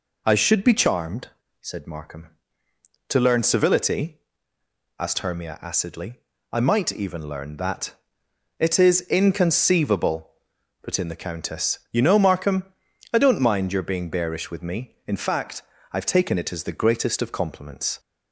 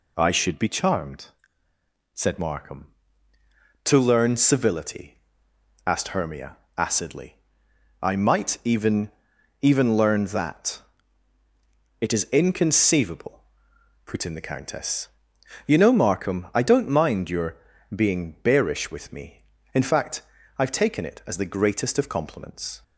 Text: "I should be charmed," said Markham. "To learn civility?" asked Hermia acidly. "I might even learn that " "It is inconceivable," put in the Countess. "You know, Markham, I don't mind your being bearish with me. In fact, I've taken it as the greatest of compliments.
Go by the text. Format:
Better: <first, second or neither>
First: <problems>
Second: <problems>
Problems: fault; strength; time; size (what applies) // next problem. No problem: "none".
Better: first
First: none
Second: pauses between "Hermia" and "acidly"; slight; at 6.5 s; 0.20 s long // says "even" twice; at 9.6 s // pauses between "your" and "being"; slight; at 17.5 s; 0.36 s long